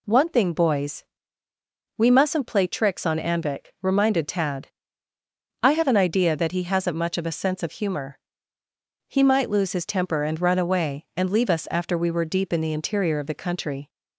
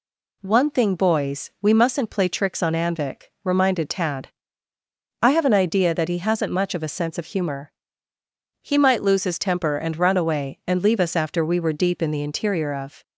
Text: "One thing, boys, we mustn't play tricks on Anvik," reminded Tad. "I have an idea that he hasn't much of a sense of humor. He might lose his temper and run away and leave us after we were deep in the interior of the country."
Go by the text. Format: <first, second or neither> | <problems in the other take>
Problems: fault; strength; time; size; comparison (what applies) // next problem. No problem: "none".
first | stops before "the country"; at 13.0 s